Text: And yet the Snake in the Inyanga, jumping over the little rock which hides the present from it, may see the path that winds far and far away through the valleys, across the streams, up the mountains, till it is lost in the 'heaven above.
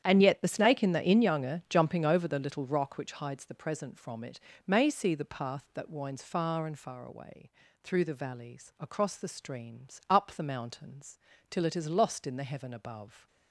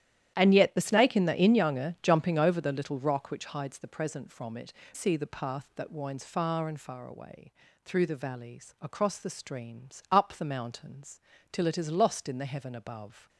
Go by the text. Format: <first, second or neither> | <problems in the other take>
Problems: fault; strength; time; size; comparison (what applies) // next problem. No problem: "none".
first | starts louder than the rest; strong; until 1.3 s; 11 dB; strong in the first // skips "may"; at 4.8 s // pauses between "away" and "through"; slight; at 7.5 s; 0.32 s long; slight in the first